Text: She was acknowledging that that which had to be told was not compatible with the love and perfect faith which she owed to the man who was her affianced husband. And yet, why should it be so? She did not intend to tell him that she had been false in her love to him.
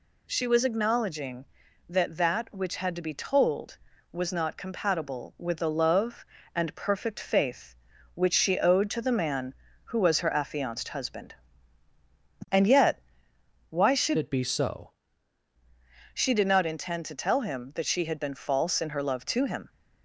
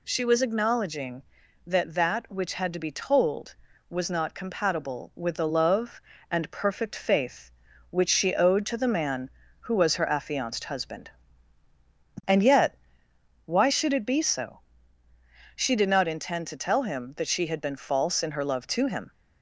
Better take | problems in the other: second | changes voice from "it" to "so"; from 14.1 to 14.8 s; 0.7 s long

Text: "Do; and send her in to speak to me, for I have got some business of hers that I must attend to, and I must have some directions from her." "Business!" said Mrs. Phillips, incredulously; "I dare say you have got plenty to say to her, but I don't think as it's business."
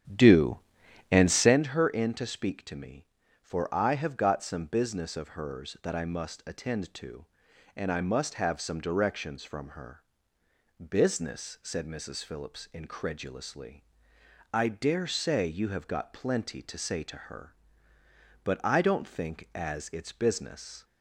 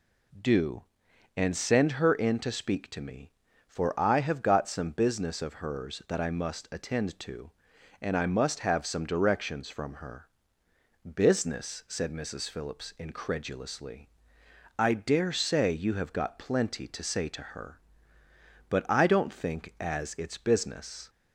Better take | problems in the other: second | starts louder than the rest; strong; until 1.6 s; 10 dB

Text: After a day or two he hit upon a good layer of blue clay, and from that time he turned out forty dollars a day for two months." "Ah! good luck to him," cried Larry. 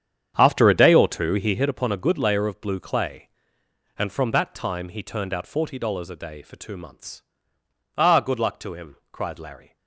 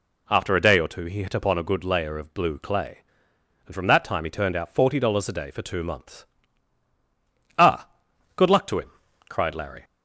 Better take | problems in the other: second | starts louder than the rest; strong; until 1.6 s; 8.5 dB

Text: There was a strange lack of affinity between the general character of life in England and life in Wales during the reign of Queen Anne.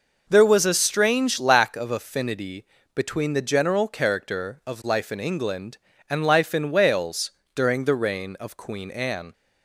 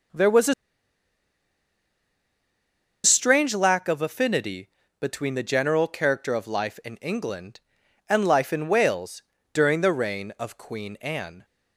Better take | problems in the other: first | pauses between "a" and "strange"; strong; at 0.5 s; 2.5 s long // pauses between "affinity" and "between"; slight; at 4.6 s; 0.32 s long; slight in the first // pauses between "Wales" and "during"; slight; at 9.2 s; 0.32 s long; slight in the first

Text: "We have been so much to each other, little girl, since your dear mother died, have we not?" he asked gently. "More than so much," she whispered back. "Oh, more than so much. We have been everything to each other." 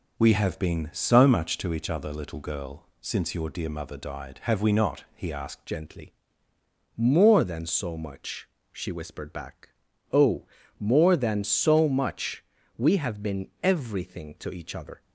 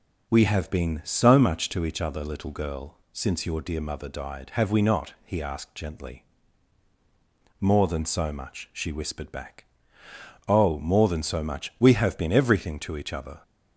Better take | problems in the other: second | changes voice at "gently"; from 5.6 s on; 9.4 s long

